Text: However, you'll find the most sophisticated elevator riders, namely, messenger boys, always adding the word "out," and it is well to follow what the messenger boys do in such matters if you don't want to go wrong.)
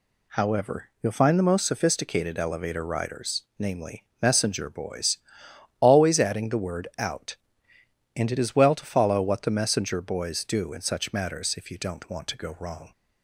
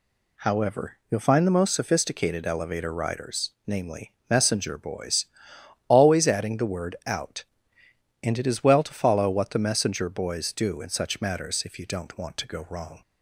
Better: neither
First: none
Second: none

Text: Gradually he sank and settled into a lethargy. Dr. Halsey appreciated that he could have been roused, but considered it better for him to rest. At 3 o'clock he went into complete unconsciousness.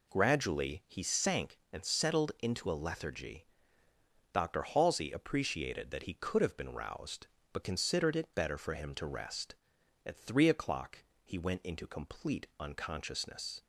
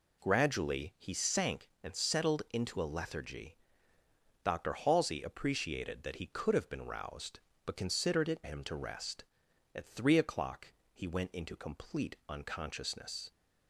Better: first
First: pauses between "o'clock" and "he"; slight; at 11.0 s; 0.20 s long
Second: skips "better for"; at 8.4 s // pauses between "o'clock" and "he"; slight; at 10.7 s; 0.20 s long

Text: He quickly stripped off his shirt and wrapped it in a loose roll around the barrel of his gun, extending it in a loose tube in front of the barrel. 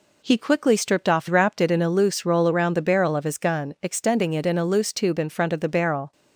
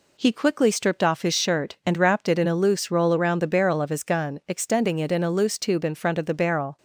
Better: second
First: skips "his shirt and"; at 1.2 s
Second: none

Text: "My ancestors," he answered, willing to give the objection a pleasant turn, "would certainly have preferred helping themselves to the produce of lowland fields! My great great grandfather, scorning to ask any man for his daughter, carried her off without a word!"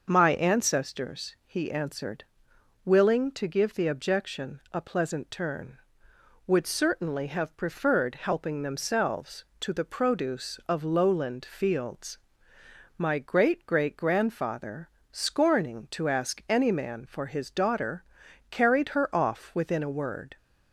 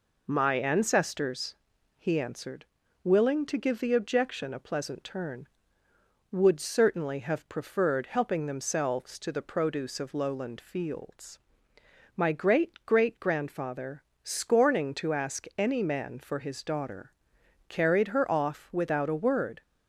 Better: second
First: says "within" for "without"; at 19.5 s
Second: none

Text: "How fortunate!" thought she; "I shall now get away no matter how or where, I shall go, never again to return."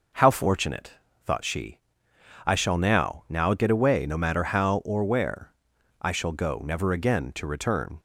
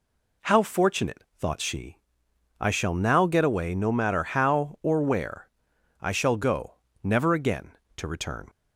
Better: second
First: says "now" twice; at 3.2 s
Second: none

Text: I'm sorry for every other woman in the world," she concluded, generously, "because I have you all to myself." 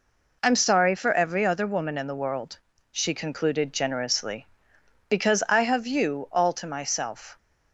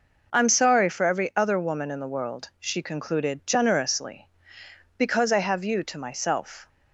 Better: first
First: none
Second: skips "all"; at 5.8 s

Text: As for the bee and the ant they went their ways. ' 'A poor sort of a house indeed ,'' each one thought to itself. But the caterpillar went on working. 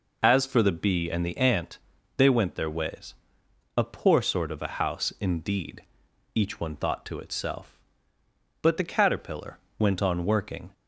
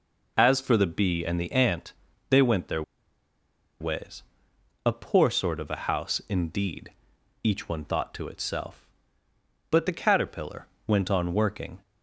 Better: first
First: pauses between "ant" and "they"; at 1.7 s; 0.38 s long // pauses between "caterpillar" and "went"; slight; at 9.5 s; 0.22 s long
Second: pauses between "ant" and "they"; slight; at 1.9 s; 0.36 s long // pauses between "their" and "ways"; at 2.8 s; 0.98 s long // pauses between "caterpillar" and "went"; slight; at 10.6 s; 0.22 s long

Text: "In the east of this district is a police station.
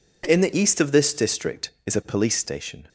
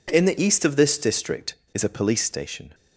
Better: neither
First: none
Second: none

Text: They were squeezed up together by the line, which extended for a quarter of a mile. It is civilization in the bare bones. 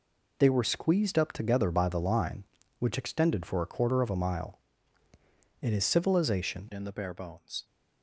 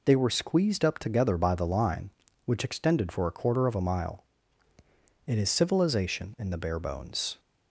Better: second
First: changes voice at "in"; from 6.7 s on; 0.9 s long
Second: none

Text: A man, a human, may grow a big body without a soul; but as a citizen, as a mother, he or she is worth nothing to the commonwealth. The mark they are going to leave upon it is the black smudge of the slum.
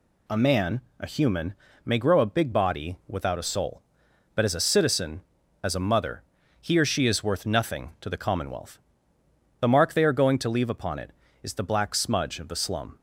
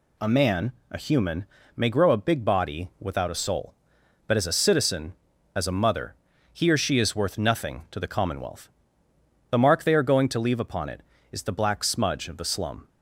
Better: neither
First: none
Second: none

